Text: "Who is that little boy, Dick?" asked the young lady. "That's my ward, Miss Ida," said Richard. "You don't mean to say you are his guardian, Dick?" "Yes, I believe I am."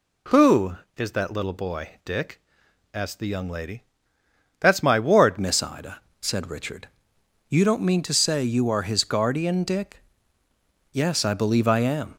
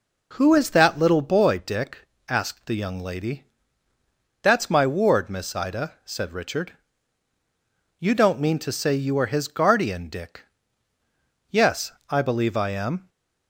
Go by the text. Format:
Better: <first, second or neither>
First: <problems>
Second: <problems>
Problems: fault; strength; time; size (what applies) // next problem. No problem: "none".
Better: second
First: changes voice at "Miss"; from 5.3 s on; 6.8 s long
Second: none